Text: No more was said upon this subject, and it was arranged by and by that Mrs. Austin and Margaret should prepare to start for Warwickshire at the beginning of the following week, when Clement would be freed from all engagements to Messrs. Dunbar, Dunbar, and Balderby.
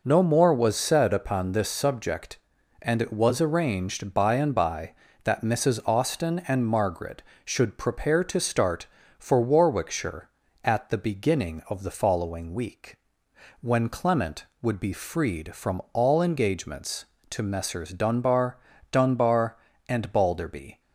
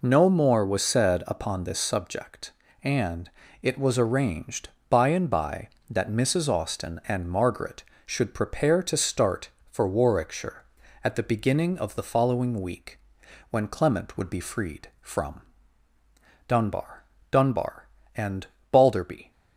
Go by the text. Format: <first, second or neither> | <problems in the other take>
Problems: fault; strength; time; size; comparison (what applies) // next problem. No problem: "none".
first | pauses between "and" and "it"; slight; at 3.2 s; 0.32 s long // skips "all engagements to Messrs"; at 15.9 s // pauses between "and" and "Balderby"; slight; at 18.4 s; 0.26 s long